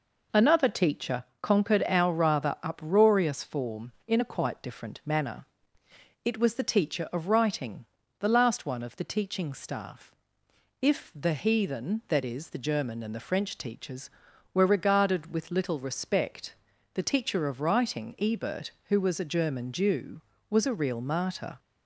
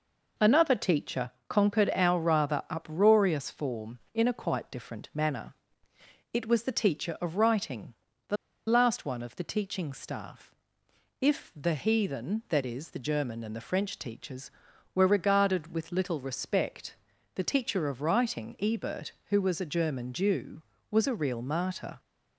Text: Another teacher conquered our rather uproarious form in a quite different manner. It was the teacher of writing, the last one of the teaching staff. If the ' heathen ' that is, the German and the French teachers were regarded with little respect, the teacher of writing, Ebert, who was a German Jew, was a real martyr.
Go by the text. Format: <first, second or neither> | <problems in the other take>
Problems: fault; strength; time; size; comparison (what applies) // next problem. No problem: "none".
first | pauses between "teacher" and "conquered"; slight; at 1.3 s; 0.18 s long; slight in the first // pauses between "the" and "last"; slight; at 8.3 s; 0.31 s long